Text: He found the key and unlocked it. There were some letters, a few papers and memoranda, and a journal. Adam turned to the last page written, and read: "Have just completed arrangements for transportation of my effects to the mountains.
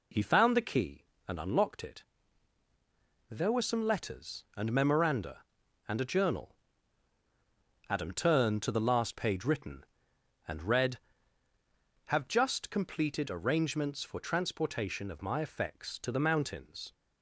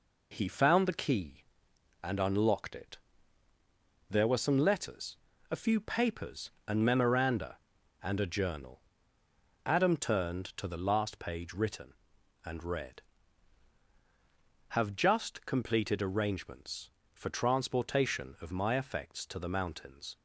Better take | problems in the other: second | skips "a few papers"; at 4.4 s

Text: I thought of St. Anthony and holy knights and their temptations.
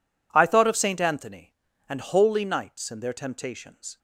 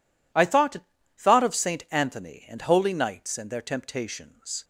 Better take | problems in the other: first | says "thought" twice; at 1.1 s

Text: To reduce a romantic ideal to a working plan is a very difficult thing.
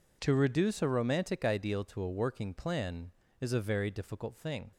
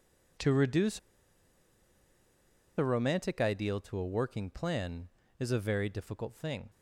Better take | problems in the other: first | pauses between "reduce" and "a"; strong; at 0.9 s; 1.7 s long

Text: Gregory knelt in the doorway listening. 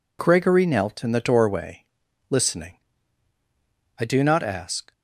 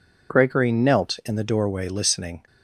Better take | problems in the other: second | pauses between "doorway" and "listening"; at 1.8 s; 0.42 s long // goes on to say "I do not ask"; noticeable; from 3.9 s on; 0.94 s long

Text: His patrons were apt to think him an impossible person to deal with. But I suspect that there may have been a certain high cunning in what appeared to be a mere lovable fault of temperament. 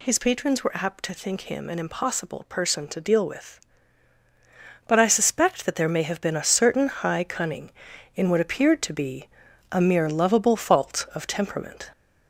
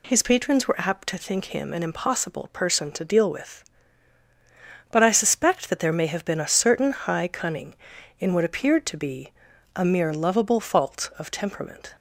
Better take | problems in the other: second | gets louder; slight; throughout; 2 dB // pauses between "be" and "a"; at 9.2 s; 0.44 s long; also in the second

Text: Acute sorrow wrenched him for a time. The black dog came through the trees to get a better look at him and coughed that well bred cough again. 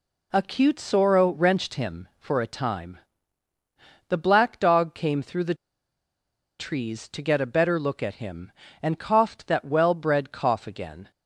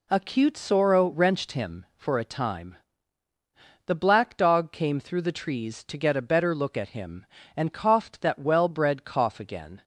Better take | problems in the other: second | pauses between "the" and "trees"; at 5.5 s; 1.0 s long

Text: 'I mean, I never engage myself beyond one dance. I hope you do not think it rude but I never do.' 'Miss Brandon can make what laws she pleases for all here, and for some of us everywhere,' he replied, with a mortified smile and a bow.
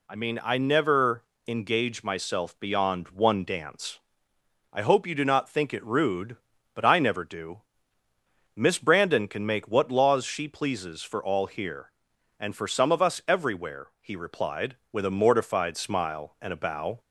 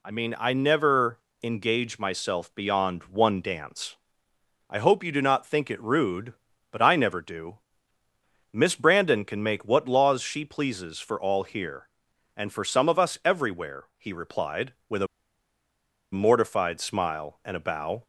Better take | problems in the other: first | pauses between "never" and "engage"; slight; at 1.1 s; 0.24 s long; slight in the first // pauses between "a" and "mortified"; at 15.0 s; 1.0 s long

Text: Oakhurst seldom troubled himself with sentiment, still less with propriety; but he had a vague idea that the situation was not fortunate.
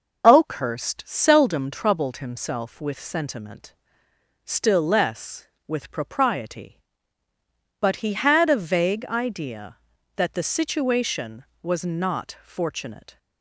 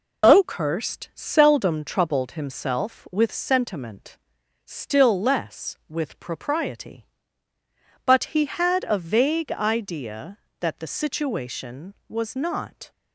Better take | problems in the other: first | stops before "fortunate"; at 12.9 s

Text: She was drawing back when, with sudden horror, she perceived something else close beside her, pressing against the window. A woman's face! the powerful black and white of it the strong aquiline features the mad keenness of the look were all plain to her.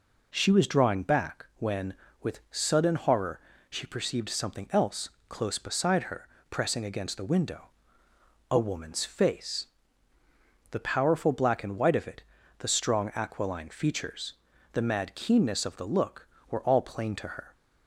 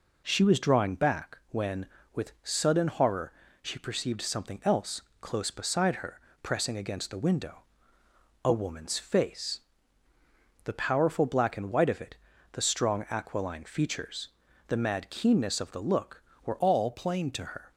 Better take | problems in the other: first | pauses between "else" and "close"; slight; at 5.0 s; 0.18 s long; slight in the first // pauses between "it" and "the"; at 12.1 s; 0.38 s long; also in the first // pauses between "features" and "the"; at 14.2 s; 0.38 s long; also in the first // changes voice from "all" to "to"; from 16.6 to 17.4 s; 0.8 s long

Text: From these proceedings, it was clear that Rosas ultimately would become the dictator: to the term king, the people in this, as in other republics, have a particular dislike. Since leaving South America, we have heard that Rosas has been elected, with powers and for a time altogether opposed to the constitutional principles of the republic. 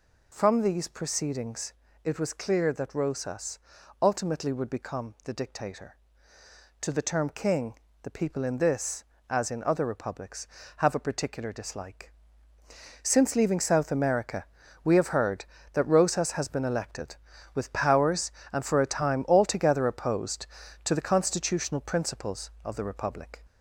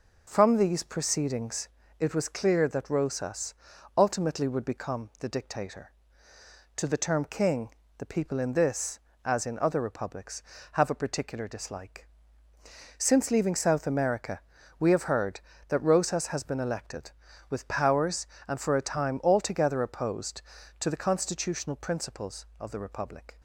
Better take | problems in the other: second | gets louder; slight; throughout; 2.5 dB // pauses between "Rosas" and "ultimately"; at 3.5 s; 0.42 s long; also in the second

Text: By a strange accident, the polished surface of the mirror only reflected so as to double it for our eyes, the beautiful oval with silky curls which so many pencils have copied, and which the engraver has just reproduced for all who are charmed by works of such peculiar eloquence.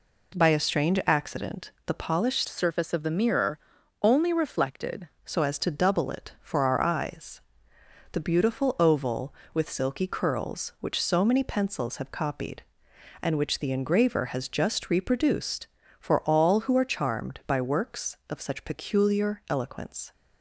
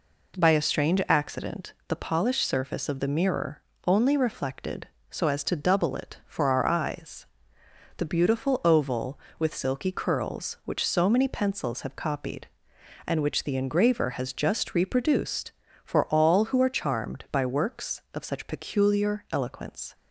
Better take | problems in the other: second | changes voice from "surface" to "reflected"; from 2.4 to 5.0 s; 2.6 s long // pauses between "mirror" and "only"; at 3.5 s; 0.42 s long; slight in the second

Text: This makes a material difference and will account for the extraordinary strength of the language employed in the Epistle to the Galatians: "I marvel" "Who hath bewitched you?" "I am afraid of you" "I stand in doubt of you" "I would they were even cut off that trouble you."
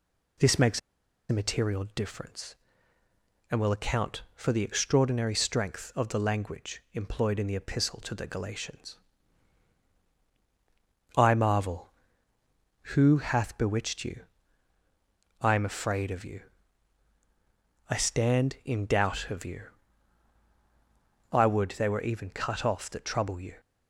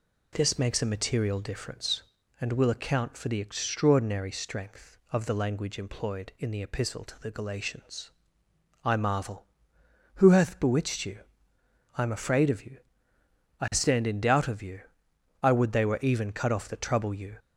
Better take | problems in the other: second | pauses between "makes" and "a"; noticeable; at 0.7 s; 0.50 s long // pauses between "you" and "I"; strong; at 16.3 s; 1.5 s long; noticeable in the second // pauses between "you" and "I"; strong; at 19.6 s; 1.7 s long; noticeable in the second

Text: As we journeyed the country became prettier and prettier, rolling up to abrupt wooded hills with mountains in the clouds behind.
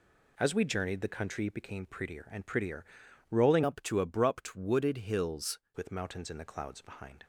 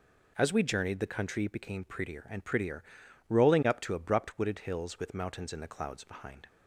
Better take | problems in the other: second | changes voice from "up" to "hills"; from 3.6 to 5.5 s; 1.9 s long

